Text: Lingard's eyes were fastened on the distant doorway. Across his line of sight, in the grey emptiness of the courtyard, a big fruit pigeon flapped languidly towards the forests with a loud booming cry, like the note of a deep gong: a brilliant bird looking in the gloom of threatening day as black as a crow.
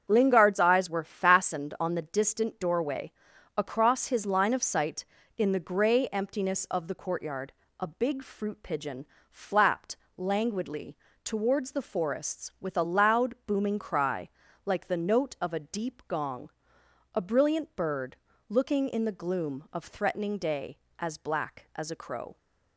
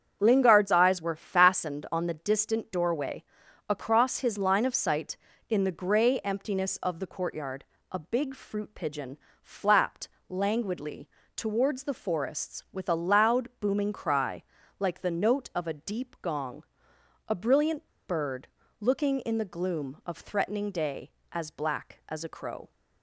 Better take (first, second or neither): first